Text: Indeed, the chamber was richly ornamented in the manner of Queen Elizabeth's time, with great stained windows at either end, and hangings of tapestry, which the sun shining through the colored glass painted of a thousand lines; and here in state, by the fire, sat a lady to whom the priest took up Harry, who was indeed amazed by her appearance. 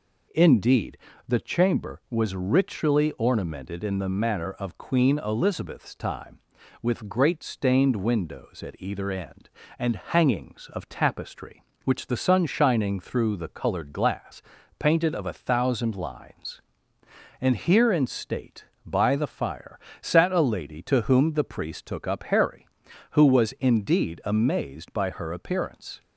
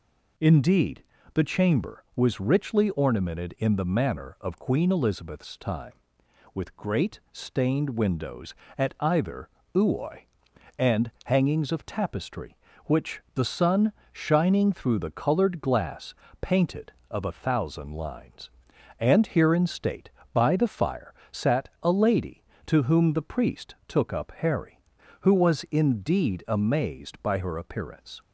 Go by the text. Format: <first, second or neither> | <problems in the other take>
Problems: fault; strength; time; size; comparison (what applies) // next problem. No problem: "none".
first | says "uoi" for "end"; at 9.7 s // pauses between "sun" and "shining"; slight; at 13.9 s; 0.20 s long // pauses between "glass" and "painted"; slight; at 16.1 s; 0.30 s long; slight in the first